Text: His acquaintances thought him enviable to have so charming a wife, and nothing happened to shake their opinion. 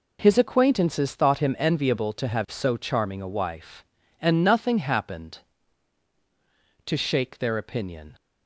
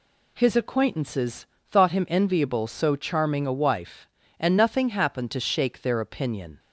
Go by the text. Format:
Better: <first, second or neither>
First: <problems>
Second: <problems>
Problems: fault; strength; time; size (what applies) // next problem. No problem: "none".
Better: first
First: none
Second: pauses between "acquaintances" and "thought"; slight; at 1.4 s; 0.22 s long // skips "to have"; at 2.6 s